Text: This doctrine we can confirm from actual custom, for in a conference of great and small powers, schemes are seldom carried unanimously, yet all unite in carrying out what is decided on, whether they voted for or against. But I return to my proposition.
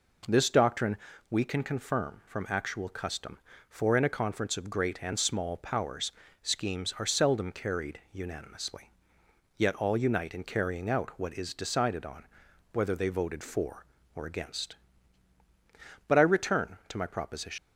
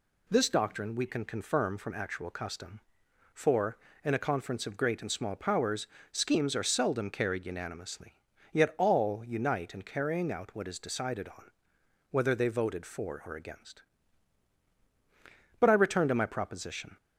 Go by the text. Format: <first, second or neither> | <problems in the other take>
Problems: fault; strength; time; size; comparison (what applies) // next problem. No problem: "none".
second | pauses between "doctrine" and "we"; slight; at 0.9 s; 0.34 s long // leaves "proposition" unfinished; at 17.5 s; 95 ms